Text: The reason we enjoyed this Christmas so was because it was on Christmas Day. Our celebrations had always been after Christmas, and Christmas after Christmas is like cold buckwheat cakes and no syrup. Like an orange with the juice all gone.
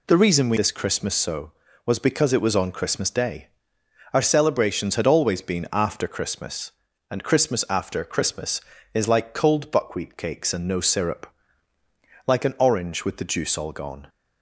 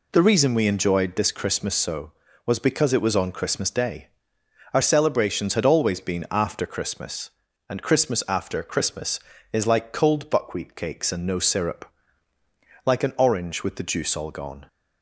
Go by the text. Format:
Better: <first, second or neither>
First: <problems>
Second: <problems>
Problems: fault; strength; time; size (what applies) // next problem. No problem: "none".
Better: second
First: skips "enjoyed"; at 0.5 s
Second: none